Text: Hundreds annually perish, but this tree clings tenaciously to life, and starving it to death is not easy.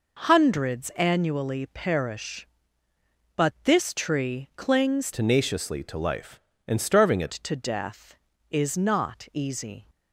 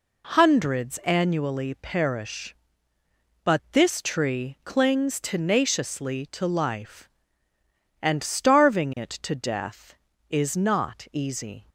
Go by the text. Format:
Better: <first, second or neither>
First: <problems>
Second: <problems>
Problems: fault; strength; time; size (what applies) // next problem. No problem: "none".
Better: second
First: changes voice from "tenaciously" to "it"; from 5.1 to 7.3 s; 2.2 s long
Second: none